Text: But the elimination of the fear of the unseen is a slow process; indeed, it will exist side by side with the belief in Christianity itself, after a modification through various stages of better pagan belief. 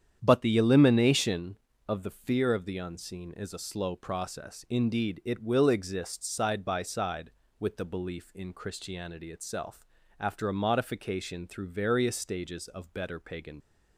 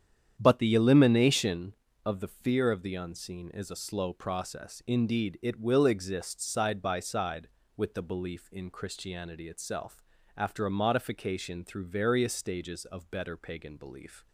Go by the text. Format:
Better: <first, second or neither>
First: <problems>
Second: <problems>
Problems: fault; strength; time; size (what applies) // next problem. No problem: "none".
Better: second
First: starts louder than the rest; strong; until 1.2 s; 9 dB // stops before "belief"; at 13.6 s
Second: starts louder than the rest; strong; until 1.3 s; 9 dB